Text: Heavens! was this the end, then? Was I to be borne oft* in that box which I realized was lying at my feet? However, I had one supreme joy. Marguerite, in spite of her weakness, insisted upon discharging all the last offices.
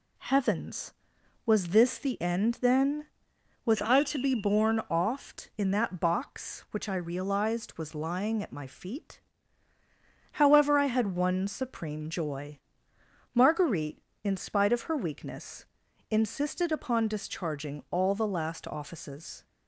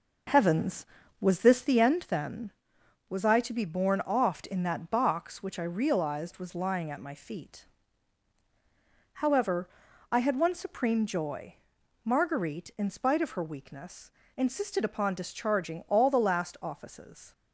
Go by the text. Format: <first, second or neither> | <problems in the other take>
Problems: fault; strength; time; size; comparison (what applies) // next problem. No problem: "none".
first | starts louder than the rest; noticeable; until 1.8 s; 5.5 dB